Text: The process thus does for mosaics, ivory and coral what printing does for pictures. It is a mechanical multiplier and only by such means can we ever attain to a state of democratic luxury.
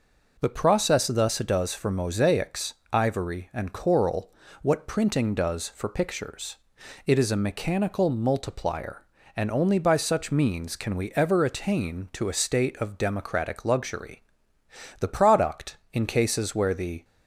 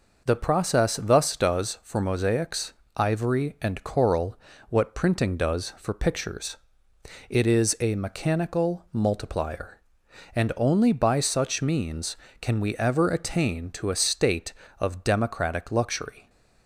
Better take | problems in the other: second | pauses between "coral" and "what"; slight; at 4.3 s; 0.30 s long; slight in the second // goes on to say "The product in cases where the"; strong; from 15.0 s on; 2.0 s long

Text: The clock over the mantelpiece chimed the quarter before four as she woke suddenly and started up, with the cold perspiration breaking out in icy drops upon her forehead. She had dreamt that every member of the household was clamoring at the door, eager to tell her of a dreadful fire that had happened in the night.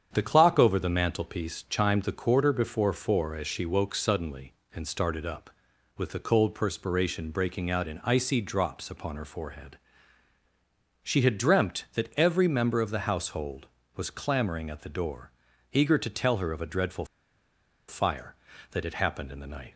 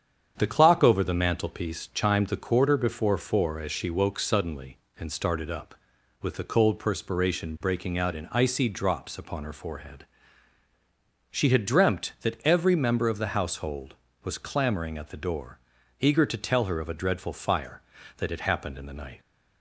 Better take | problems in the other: second | starts louder than the rest; strong; until 1.1 s; 8 dB; strong in the second // pauses between "dreadful" and "fire"; noticeable; at 17.0 s; 0.82 s long

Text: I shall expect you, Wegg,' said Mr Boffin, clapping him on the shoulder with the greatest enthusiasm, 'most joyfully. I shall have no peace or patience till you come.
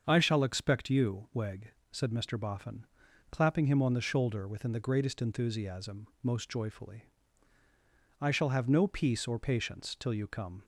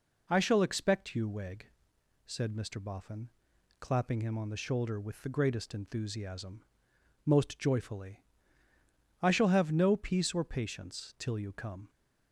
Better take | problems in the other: second | starts louder than the rest; until 1.0 s; 7 dB // says "within" for "with"; at 4.4 s

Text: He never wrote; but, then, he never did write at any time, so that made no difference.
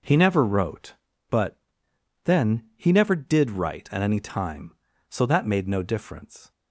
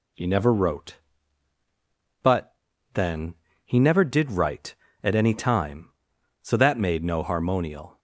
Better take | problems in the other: first | says "harmonial" for "difference"; at 7.2 s

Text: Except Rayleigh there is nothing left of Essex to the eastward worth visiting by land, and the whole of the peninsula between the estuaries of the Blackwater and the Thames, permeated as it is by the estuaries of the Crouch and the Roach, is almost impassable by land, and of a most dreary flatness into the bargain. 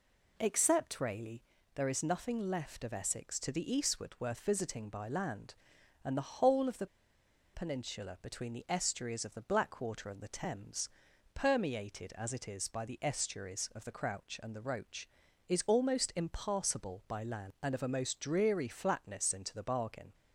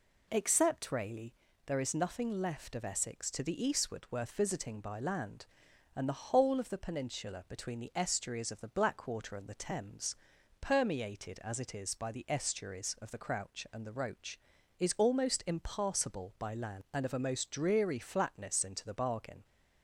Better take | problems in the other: second | pauses between "Rayleigh" and "there"; slight; at 1.4 s; 0.36 s long; slight in the second // pauses between "the" and "peninsula"; noticeable; at 6.8 s; 0.67 s long

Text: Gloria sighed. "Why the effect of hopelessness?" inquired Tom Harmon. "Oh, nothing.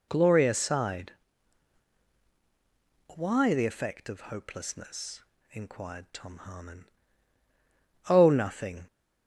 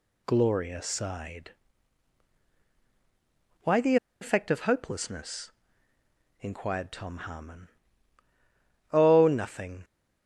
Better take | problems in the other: first | pauses between "the" and "effect"; slight; at 3.9 s; 0.25 s long

